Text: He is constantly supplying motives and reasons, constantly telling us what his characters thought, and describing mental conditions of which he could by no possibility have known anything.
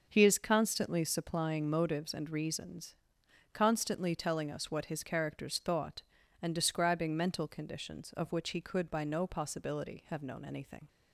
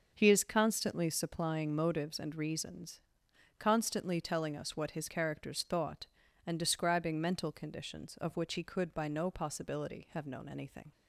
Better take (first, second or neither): neither